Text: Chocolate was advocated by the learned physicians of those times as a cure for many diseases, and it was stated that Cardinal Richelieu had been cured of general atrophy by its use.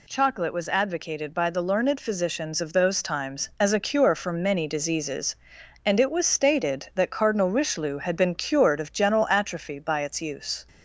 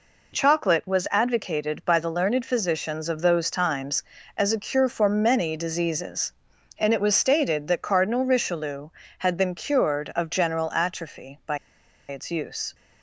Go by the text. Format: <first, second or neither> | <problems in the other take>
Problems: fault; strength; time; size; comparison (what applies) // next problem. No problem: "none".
first | pauses between "by" and "its"; noticeable; at 11.5 s; 0.51 s long